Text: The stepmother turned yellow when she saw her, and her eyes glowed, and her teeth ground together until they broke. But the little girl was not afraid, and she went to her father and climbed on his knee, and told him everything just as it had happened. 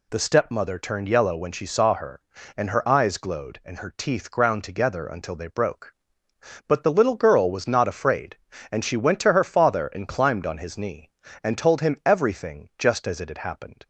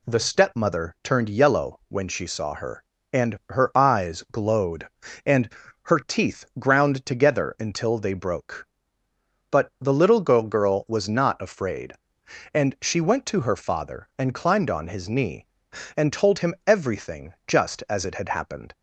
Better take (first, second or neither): first